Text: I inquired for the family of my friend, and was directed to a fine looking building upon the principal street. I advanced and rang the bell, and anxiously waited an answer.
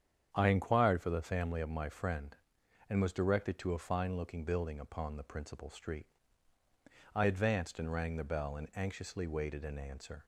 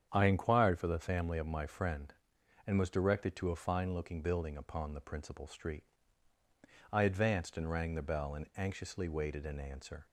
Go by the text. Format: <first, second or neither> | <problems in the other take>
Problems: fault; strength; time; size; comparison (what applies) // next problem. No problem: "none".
neither | starts louder than the rest; strong; the same in both